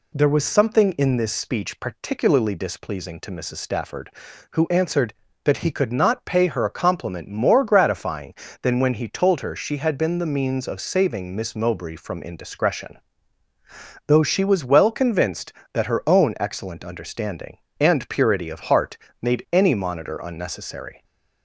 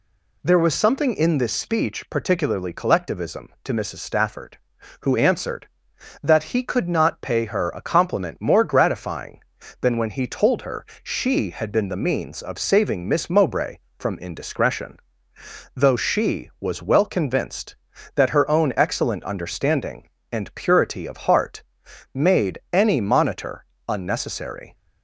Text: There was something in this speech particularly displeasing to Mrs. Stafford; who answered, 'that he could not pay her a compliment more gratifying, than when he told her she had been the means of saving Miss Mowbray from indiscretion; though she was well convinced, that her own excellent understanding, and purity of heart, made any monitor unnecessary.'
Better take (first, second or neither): first